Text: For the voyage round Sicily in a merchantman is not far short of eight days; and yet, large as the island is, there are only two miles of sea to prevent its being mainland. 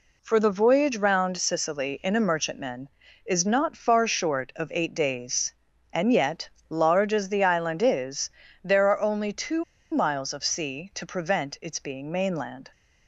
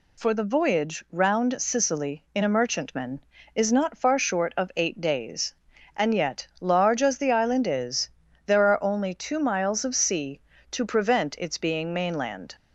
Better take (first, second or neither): second